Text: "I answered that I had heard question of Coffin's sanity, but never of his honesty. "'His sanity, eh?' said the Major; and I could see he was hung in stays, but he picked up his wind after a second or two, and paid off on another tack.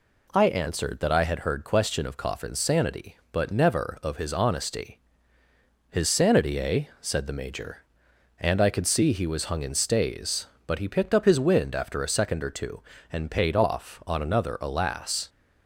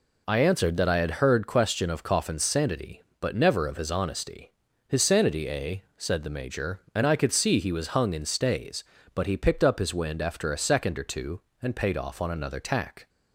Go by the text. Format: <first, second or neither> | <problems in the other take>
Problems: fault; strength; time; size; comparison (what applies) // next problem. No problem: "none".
second | says "alas" for "tack"; at 14.6 s